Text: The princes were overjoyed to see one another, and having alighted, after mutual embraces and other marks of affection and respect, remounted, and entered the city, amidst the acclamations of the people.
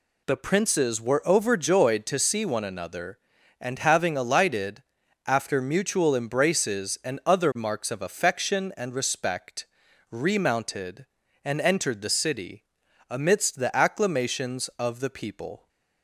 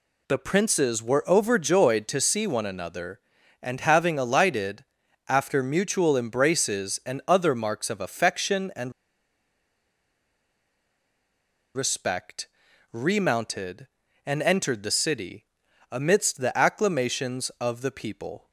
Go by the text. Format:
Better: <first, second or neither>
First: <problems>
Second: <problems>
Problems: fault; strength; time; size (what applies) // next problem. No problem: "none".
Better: first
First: none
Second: pauses between "and" and "respect"; strong; at 8.9 s; 2.8 s long